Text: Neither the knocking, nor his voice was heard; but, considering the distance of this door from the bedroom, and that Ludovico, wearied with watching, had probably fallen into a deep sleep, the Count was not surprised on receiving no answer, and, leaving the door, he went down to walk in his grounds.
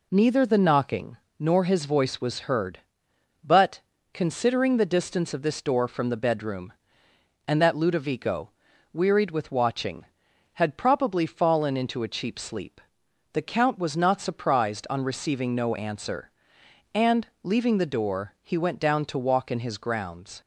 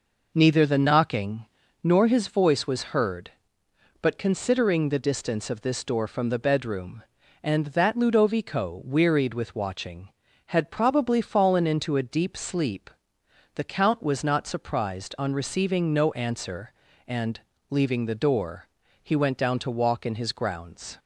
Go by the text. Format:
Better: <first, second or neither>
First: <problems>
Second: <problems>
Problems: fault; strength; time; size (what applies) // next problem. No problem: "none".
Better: second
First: says "cheap" for "deep"; at 12.0 s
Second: none